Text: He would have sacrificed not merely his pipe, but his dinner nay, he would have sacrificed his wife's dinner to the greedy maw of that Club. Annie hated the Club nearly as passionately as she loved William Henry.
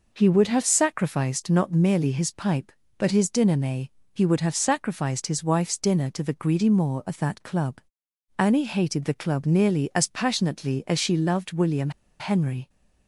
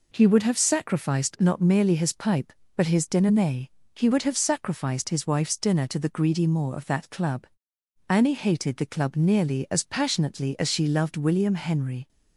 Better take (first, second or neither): second